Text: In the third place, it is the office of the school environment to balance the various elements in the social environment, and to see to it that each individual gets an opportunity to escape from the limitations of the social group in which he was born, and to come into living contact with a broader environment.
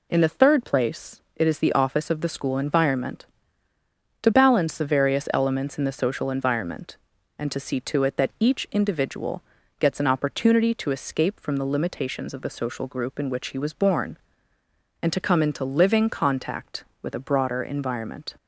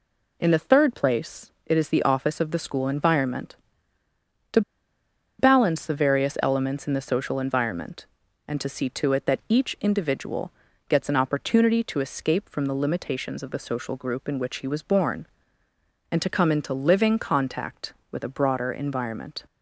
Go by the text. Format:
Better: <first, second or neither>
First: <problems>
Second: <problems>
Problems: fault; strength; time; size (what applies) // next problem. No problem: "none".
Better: first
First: pauses between "individual" and "gets"; at 9.4 s; 0.38 s long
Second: pauses between "to" and "balance"; noticeable; at 4.6 s; 0.78 s long // pauses between "individual" and "gets"; at 10.5 s; 0.38 s long